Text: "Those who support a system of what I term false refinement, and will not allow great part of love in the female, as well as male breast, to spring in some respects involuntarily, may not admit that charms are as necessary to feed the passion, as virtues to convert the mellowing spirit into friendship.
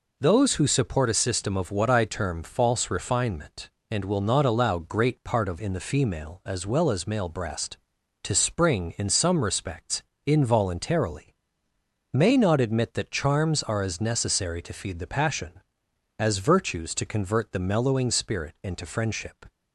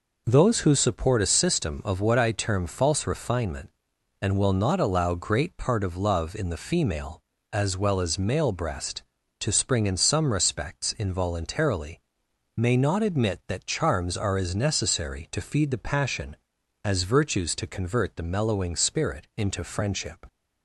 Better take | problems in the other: second | skips "love"; at 5.5 s // pauses between "respects" and "involuntarily"; slight; at 10.0 s; 0.24 s long

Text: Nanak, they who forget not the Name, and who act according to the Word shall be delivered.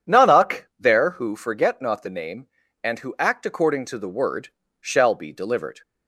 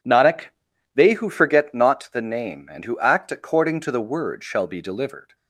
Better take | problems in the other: second | says "there" for "they"; at 0.7 s // pauses between "Word" and "shall"; slight; at 4.4 s; 0.32 s long

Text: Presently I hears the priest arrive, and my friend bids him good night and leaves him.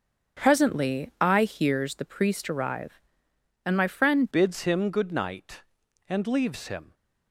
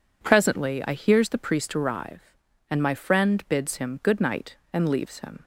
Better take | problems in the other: second | starts louder than the rest; until 1.4 s; 7 dB // changes voice at "bids"; from 4.3 s on; 2.6 s long

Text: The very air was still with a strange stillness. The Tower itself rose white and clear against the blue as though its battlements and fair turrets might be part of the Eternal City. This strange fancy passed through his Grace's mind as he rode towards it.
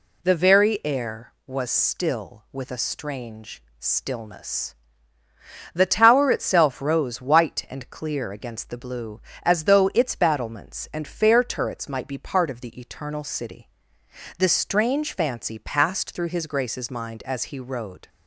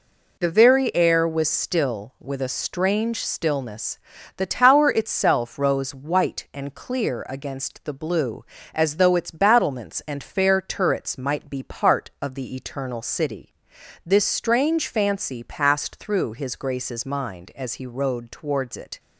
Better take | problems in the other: second | pauses between "strange" and "stillness"; slight; at 3.6 s; 0.16 s long // stops before "towards it"; at 18.0 s

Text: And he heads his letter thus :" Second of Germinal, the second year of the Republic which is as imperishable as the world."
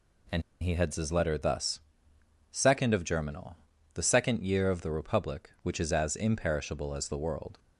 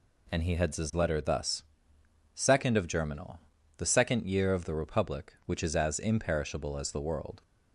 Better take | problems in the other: second | pauses between "And" and "he"; slight; at 0.4 s; 0.20 s long

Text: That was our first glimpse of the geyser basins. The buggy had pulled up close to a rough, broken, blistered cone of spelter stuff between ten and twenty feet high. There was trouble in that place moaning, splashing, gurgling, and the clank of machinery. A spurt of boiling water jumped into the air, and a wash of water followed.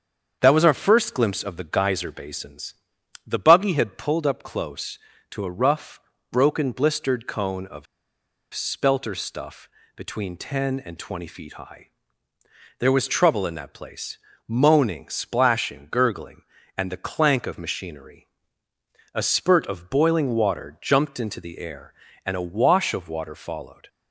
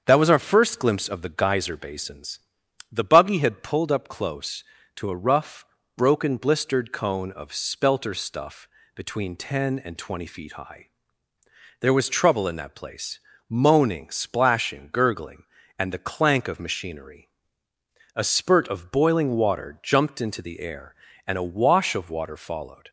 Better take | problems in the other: second | starts louder than the rest; strong; until 1.4 s; 7.5 dB; strong in the second // pauses between "of" and "spelter"; noticeable; at 7.8 s; 0.68 s long // pauses between "stuff" and "between"; slight; at 9.6 s; 0.28 s long; slight in the second // pauses between "place" and "moaning"; slight; at 14.1 s; 0.28 s long; slight in the second

